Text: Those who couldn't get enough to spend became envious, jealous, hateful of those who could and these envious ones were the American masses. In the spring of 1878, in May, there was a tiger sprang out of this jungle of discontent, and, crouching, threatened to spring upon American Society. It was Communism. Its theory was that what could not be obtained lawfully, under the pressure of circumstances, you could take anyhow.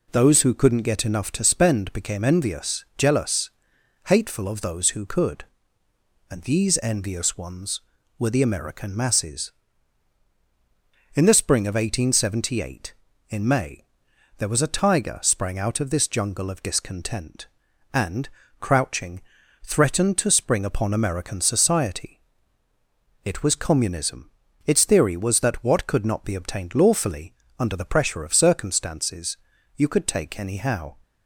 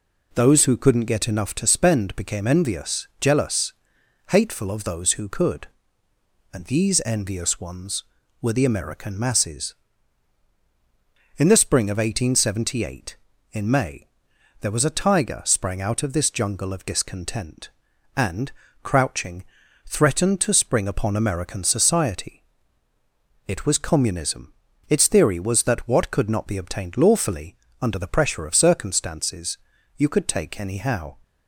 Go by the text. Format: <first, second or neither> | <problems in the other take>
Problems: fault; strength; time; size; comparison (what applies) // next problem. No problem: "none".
neither | none